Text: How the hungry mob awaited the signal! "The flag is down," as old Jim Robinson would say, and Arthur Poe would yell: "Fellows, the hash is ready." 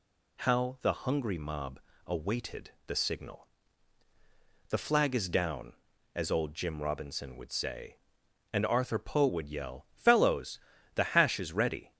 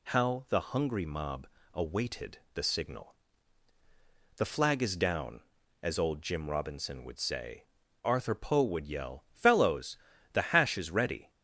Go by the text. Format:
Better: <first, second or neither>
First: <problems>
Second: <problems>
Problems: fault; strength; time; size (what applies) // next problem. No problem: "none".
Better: first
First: pauses between "mob" and "awaited"; slight; at 1.7 s; 0.28 s long // pauses between "awaited" and "the"; slight; at 2.7 s; 0.16 s long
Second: pauses between "mob" and "awaited"; slight; at 1.4 s; 0.28 s long // pauses between "awaited" and "the"; slight; at 2.3 s; 0.16 s long // skips "and"; at 7.8 s